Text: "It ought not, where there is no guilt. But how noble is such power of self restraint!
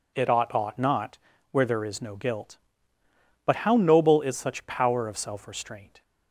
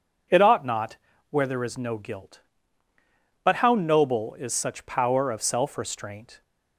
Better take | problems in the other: second | says "ought" twice; at 0.5 s

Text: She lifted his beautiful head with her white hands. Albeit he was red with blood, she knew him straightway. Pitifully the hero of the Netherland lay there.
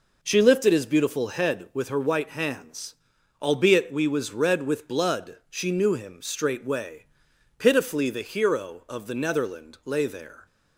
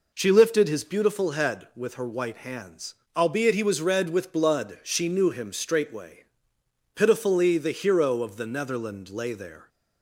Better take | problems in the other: second | says "we" for "he"; at 3.9 s

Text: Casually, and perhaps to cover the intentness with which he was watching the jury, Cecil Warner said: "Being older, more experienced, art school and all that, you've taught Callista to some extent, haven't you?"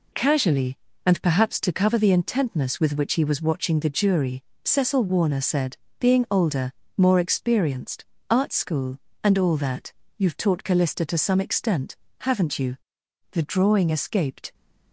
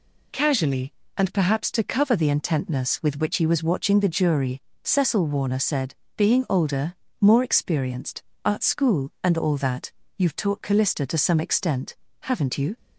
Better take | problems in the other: second | goes on to say "The drawing escaped"; noticeable; from 13.3 s on; 1.2 s long

